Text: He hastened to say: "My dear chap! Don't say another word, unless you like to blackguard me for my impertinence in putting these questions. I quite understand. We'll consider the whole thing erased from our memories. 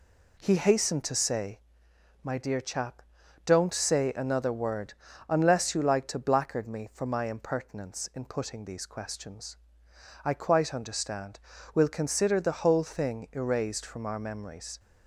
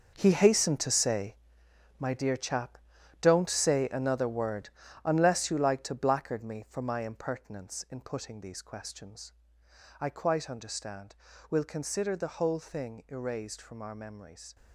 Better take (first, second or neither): first